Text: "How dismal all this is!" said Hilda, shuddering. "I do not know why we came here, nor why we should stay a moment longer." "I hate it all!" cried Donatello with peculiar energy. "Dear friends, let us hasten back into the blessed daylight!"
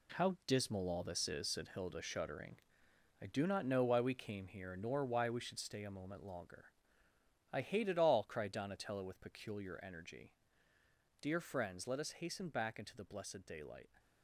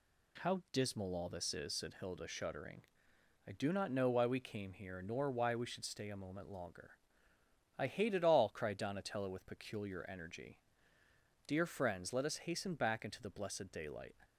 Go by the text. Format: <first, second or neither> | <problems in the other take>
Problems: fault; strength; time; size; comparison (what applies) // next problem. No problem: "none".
second | gets quieter; strong; throughout; 9 dB